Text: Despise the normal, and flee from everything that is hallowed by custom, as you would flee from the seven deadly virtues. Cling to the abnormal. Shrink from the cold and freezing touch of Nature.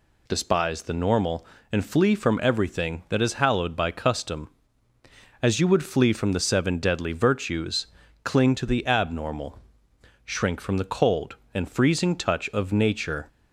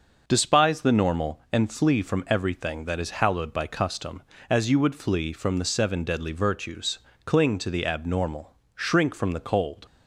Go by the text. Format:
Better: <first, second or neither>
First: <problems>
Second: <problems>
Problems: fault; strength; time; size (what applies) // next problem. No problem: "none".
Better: first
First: none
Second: starts louder than the rest; noticeable; until 1.2 s; 6 dB // stops before "and freezing touch of Nature"; at 9.8 s